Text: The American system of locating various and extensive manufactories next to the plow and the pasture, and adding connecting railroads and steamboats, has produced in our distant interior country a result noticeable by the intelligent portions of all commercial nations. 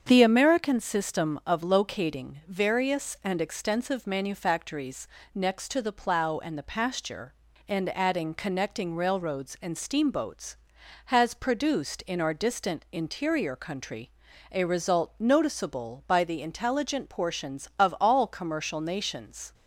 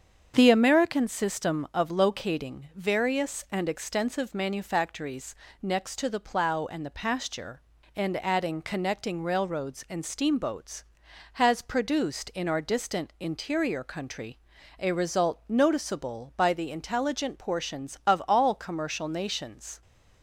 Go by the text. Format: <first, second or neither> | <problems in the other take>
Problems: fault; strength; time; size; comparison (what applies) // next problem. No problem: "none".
neither | starts louder than the rest; strong; the same in both // pauses between "manufactories" and "next"; slight; the same in both // pauses between "country" and "a"; the same in both